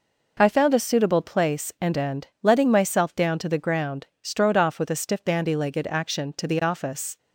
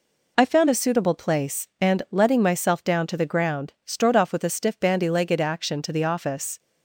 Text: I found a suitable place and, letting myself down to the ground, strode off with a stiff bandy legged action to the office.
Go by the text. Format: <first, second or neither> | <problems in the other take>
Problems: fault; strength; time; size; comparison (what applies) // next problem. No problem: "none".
second | says "and" twice; at 1.9 s